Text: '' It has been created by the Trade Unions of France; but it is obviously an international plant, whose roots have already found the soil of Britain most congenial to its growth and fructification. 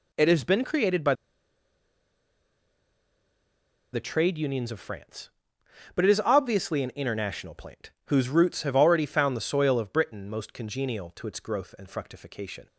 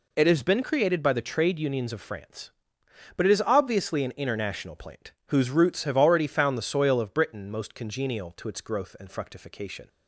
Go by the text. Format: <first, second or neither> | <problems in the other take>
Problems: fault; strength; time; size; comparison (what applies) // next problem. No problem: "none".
second | pauses between "by" and "the"; strong; at 1.1 s; 2.7 s long